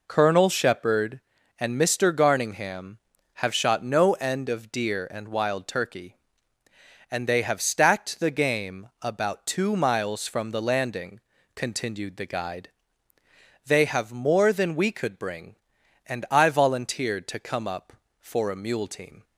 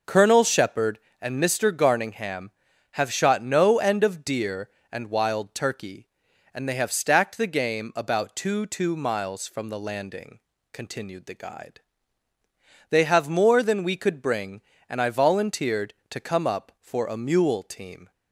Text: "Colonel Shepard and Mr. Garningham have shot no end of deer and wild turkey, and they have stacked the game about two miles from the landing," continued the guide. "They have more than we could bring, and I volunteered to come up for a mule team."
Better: first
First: none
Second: says "two" twice; at 8.6 s

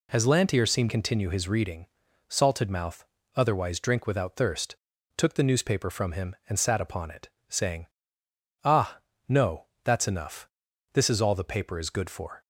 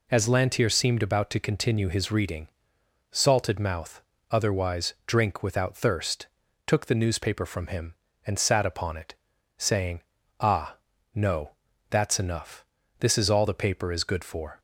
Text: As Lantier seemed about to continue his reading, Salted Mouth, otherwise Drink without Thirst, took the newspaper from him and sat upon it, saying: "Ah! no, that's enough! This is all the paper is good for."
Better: second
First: skips "about to"; at 0.8 s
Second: none

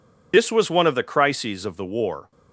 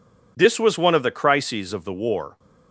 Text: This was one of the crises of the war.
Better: second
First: loses the start of "This"; at 0.3 s; 45 ms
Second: none

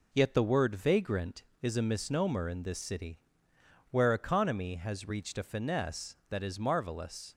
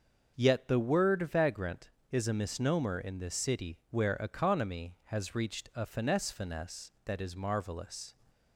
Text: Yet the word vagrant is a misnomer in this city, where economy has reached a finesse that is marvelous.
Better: first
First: none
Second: starts louder than the rest; until 1.4 s; 6.5 dB // says "finesse" twice; at 6.3 s

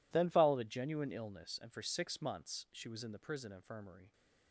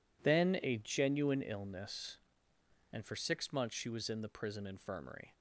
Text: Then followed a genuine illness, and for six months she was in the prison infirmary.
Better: first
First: none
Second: skips "followed"; at 0.6 s

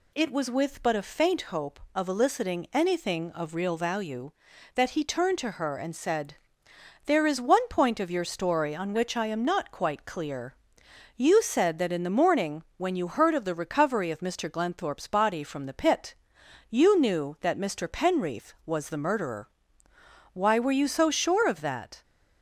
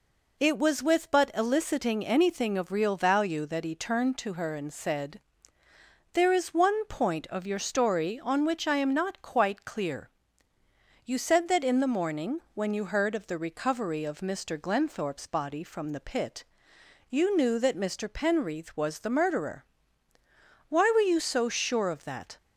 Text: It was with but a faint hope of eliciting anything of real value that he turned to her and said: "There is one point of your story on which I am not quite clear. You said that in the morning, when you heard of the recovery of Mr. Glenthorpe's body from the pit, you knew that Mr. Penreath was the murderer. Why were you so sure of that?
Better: first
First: none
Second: skips "a faint hope of"; at 1.3 s

